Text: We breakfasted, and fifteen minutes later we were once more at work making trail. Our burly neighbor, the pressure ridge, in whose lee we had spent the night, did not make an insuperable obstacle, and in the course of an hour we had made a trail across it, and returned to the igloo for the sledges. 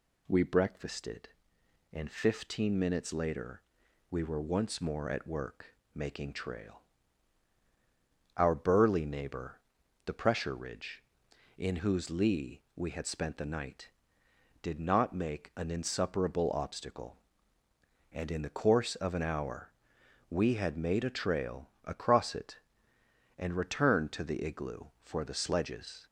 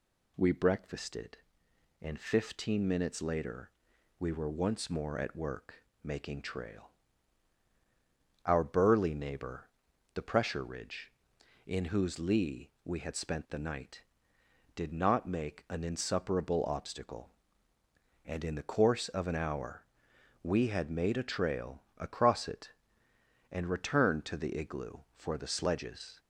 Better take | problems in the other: neither | pauses between "later" and "we"; noticeable; the same in both // pauses between "work" and "making"; slight; the same in both // pauses between "hour" and "we"; noticeable; the same in both // pauses between "trail" and "across"; slight; the same in both

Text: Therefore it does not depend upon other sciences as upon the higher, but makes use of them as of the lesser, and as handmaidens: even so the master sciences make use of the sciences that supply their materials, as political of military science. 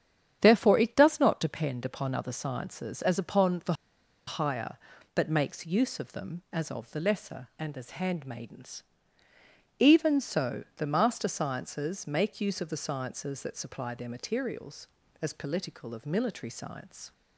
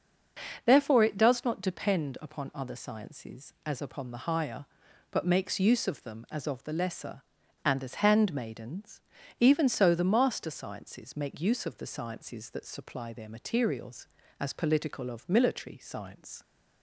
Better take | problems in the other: second | starts louder than the rest; strong; until 1.4 s; 9 dB; also in the second // pauses between "the" and "higher"; noticeable; at 3.7 s; 0.54 s long

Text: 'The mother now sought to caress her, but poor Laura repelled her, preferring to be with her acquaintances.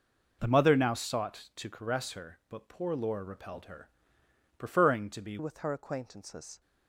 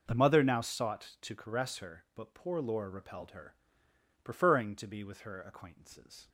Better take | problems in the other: second | changes voice at "with"; from 5.3 s on; 1.2 s long

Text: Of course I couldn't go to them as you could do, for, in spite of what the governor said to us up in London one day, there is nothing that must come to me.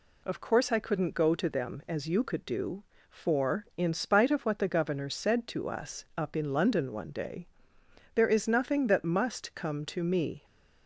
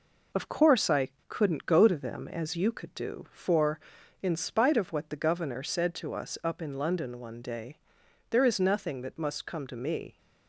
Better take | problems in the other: first | gets quieter; noticeable; throughout; 4 dB // pauses between "I" and "couldn't"; slight; at 1.1 s; 0.18 s long

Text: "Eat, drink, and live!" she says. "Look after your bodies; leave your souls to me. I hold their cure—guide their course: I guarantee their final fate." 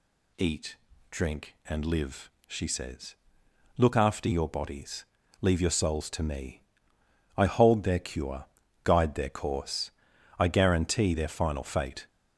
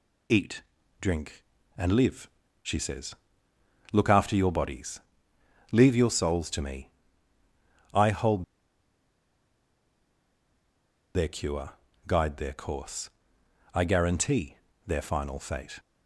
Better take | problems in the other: first | pauses between "hold" and "their"; strong; at 8.4 s; 2.7 s long // pauses between "guarantee" and "their"; slight; at 14.5 s; 0.28 s long

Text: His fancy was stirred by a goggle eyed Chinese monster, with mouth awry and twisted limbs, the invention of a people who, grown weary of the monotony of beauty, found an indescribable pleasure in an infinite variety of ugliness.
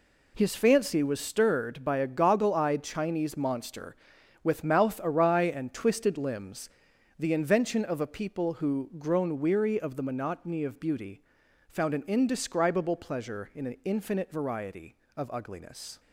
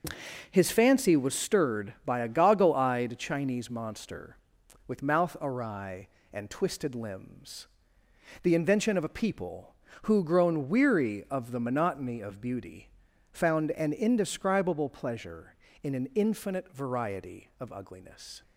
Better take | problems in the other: neither | none

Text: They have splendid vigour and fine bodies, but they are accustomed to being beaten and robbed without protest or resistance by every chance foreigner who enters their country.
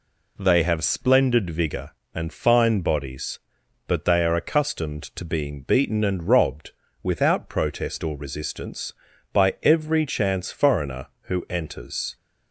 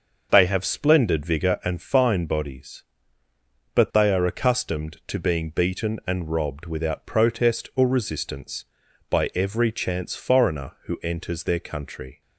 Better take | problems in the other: second | pauses between "robbed" and "without"; slight; at 6.7 s; 0.32 s long // stops before "their country"; at 12.1 s

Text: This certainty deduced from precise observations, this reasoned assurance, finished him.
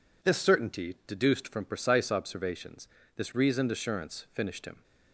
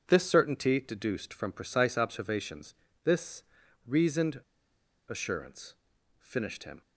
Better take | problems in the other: first | pauses between "this" and "reasoned"; at 3.4 s; 0.42 s long // pauses between "reasoned" and "assurance"; noticeable; at 4.3 s; 0.70 s long

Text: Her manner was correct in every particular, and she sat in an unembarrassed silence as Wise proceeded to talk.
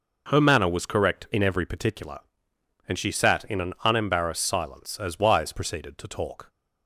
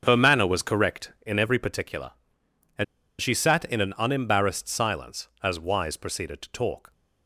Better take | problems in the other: first | starts louder than the rest; until 1.0 s; 7 dB // pauses between "and" and "she"; slight; at 2.8 s; 0.35 s long

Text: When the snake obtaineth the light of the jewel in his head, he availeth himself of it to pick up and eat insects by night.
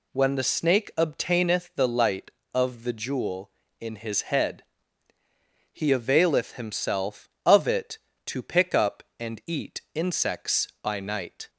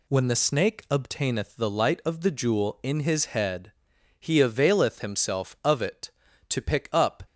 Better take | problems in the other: first | stops before "and eat insects by night"; at 7.2 s

